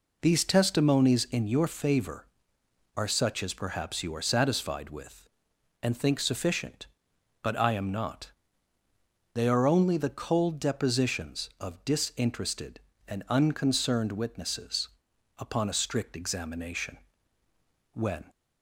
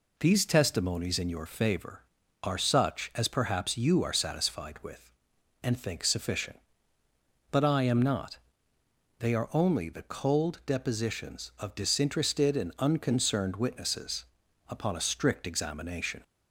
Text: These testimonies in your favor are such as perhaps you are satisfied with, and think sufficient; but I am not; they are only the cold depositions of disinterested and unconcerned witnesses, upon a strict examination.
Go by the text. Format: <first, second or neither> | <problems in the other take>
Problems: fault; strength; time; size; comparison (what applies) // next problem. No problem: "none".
second | goes on to say "When"; slight; from 17.9 s on; 0.32 s long